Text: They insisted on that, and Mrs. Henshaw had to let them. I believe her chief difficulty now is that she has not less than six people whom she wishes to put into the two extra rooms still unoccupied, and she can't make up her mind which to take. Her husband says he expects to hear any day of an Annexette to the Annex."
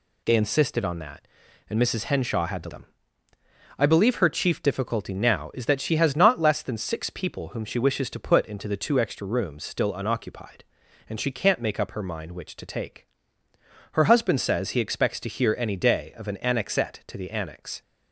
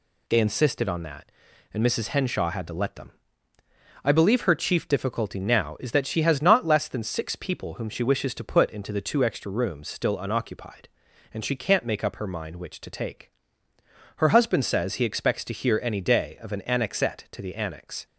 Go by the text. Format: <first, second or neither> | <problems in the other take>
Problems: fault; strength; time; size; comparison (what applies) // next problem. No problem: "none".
second | skips "let"; at 2.6 s